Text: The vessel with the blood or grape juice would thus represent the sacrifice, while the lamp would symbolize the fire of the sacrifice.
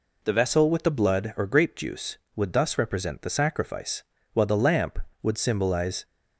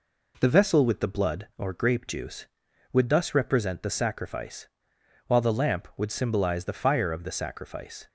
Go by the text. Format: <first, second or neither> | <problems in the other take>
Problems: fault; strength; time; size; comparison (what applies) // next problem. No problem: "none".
second | stops before "the fire of the sacrifice"; at 6.0 s